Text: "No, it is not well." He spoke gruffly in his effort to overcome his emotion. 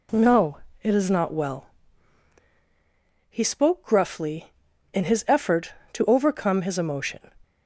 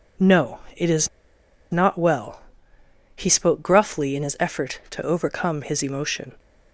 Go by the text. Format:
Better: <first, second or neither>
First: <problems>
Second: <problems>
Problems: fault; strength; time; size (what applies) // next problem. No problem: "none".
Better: first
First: none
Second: pauses between "is" and "not"; noticeable; at 1.0 s; 0.63 s long